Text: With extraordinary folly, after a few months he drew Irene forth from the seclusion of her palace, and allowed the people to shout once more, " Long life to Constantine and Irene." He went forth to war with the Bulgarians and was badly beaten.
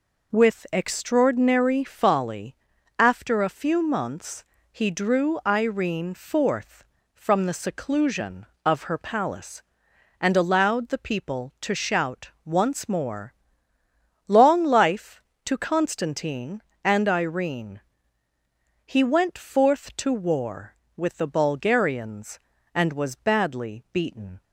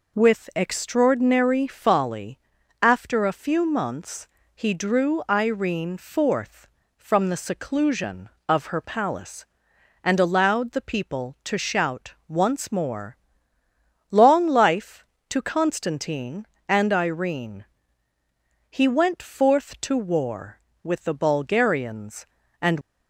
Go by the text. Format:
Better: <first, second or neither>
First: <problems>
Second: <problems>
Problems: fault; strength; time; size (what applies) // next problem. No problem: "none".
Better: first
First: pauses between "months" and "he"; slight; at 4.4 s; 0.26 s long // pauses between "shout" and "once"; slight; at 12.2 s; 0.16 s long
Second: pauses between "months" and "he"; slight; at 4.2 s; 0.26 s long // pauses between "shout" and "once"; slight; at 12.1 s; 0.16 s long // stops before "was badly beaten"; at 22.8 s